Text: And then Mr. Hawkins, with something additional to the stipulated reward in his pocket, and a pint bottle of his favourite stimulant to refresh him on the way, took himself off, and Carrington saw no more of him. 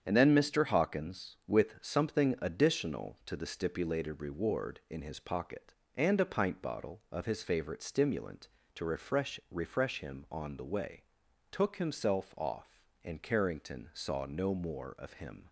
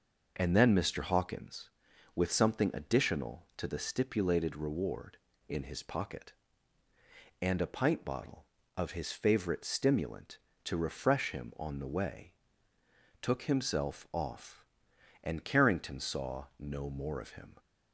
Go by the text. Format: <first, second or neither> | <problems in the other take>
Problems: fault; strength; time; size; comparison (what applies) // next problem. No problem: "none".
second | starts louder than the rest; strong; until 1.0 s; 8 dB // says "refresh" twice; at 9.4 s